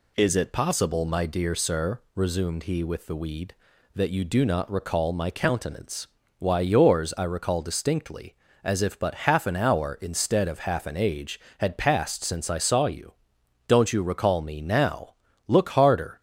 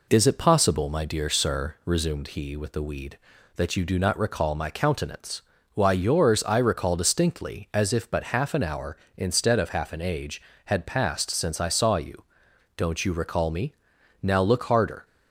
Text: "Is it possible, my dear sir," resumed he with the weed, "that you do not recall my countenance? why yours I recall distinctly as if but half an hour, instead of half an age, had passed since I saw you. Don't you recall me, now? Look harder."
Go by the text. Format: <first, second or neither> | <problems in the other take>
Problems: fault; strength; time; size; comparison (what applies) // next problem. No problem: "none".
neither | none